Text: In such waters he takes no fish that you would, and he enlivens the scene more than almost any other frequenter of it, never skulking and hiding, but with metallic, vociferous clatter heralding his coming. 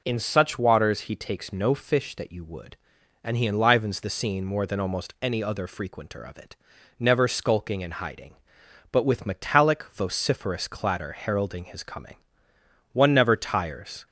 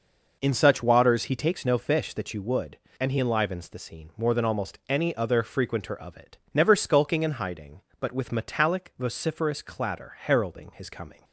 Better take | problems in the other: second | goes on to say "One never tires"; noticeable; from 12.9 s on; 1.1 s long

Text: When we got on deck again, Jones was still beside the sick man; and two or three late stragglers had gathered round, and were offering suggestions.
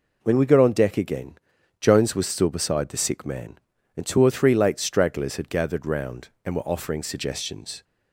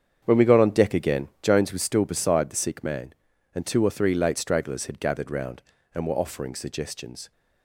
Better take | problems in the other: first | starts louder than the rest; strong; until 1.6 s; 8 dB

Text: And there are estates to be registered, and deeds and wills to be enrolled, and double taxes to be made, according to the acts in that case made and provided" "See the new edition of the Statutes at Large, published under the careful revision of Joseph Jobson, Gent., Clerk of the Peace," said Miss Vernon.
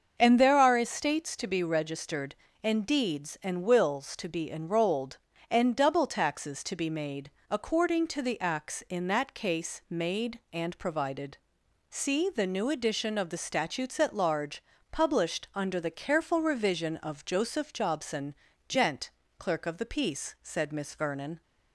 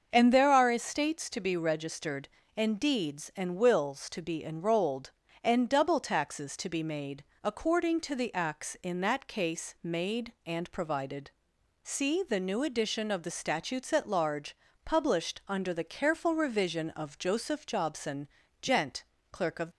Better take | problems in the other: first | starts louder than the rest; until 1.1 s; 6.5 dB; also in the first // pauses between "provided" and "See"; noticeable; at 11.3 s; 0.52 s long; noticeable in the first // stops before "the Peace said Miss Vernon"; at 19.7 s

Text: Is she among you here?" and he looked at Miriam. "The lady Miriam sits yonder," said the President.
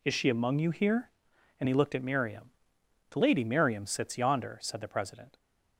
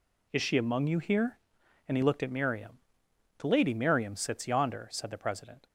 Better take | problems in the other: neither | none

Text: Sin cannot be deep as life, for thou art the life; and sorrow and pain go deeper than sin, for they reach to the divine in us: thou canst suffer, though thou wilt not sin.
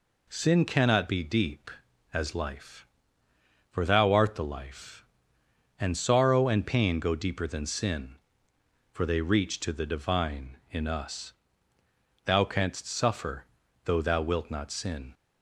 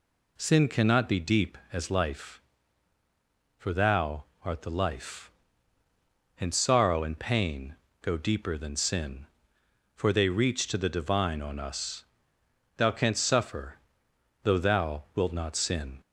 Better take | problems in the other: first | pauses between "thou" and "art"; slight; at 4.2 s; 0.18 s long // pauses between "pain" and "go"; slight; at 7.7 s; 0.26 s long // says "on" for "in"; at 11.3 s

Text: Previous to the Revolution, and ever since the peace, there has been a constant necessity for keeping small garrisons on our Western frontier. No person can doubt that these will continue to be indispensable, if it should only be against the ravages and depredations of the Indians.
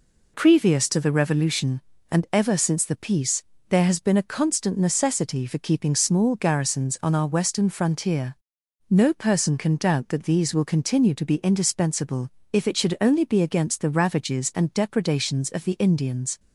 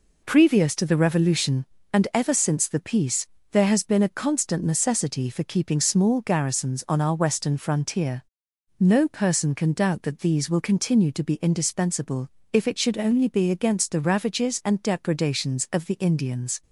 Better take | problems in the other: neither | none

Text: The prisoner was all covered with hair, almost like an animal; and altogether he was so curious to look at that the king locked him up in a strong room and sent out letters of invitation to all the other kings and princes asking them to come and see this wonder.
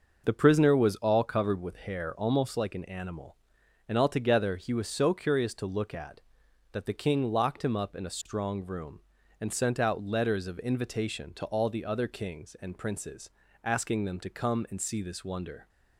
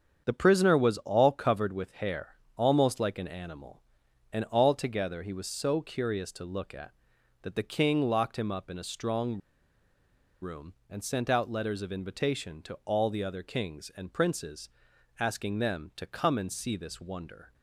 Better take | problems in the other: first | starts louder than the rest; strong; until 1.2 s; 7.5 dB; noticeable in the first // pauses between "strong" and "room"; at 9.3 s; 1.0 s long // pauses between "princes" and "asking"; noticeable; at 14.6 s; 0.50 s long; slight in the first

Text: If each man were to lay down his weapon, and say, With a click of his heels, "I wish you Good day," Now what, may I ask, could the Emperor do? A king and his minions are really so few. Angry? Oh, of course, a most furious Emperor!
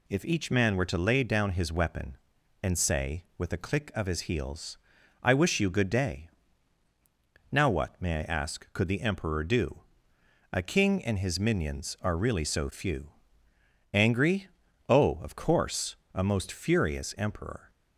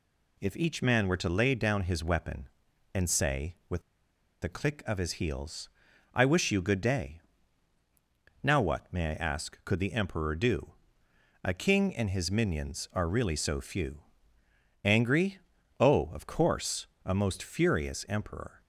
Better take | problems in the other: first | pauses between "With" and "a"; noticeable; at 3.8 s; 0.61 s long

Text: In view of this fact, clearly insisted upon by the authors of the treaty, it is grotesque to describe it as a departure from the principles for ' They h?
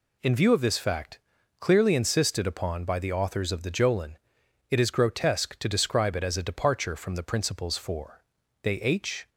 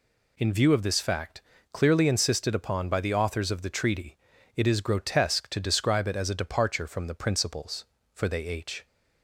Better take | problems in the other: second | says "jolin" for "treaty"; at 3.7 s

